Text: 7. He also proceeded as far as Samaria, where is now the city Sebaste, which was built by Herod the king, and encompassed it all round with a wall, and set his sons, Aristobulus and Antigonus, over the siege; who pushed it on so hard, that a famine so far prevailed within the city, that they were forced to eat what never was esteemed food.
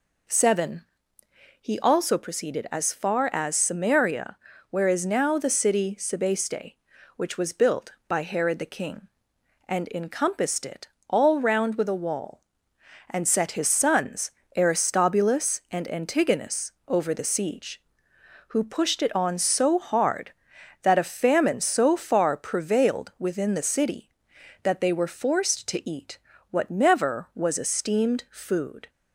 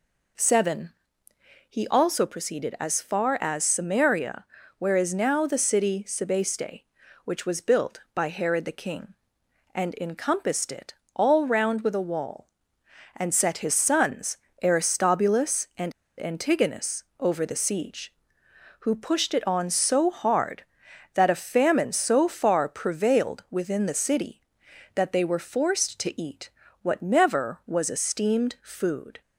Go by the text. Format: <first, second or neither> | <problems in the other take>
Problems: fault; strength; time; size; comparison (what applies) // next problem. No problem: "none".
first | pauses between "it" and "all"; slight; at 10.9 s; 0.22 s long; slight in the first // pauses between "and" and "Antigonus"; slight; at 15.9 s; 0.26 s long // pauses between "eat" and "what"; slight; at 26.5 s; 0.32 s long; slight in the first